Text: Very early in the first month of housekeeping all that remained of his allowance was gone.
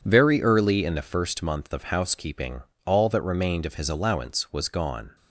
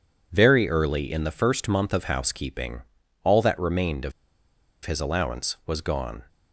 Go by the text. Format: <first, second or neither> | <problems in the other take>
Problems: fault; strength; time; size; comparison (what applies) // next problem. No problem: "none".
first | pauses between "housekeeping" and "all"; at 2.8 s; 0.40 s long; slight in the first // pauses between "of" and "his"; noticeable; at 4.1 s; 0.73 s long